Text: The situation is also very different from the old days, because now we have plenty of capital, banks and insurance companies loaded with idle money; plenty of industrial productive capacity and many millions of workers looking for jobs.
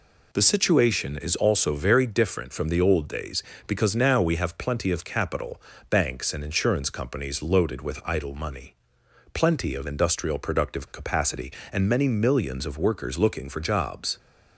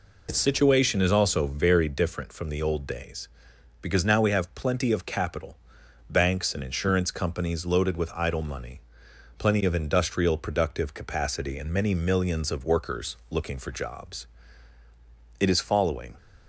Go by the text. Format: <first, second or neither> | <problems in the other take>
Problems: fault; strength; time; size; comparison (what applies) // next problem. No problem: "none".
first | goes on to say "It is following"; noticeable; from 15.4 s on; 0.76 s long